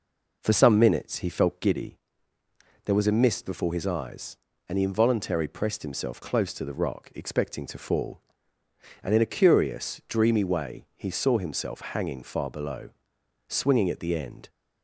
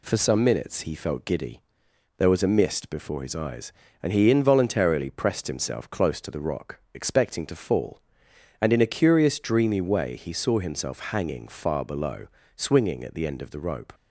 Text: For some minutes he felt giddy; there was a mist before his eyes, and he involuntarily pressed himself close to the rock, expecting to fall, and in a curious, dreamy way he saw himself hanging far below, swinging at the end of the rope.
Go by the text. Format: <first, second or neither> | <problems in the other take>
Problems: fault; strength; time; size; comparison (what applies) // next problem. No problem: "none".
second | stops before "of the rope"; at 14.4 s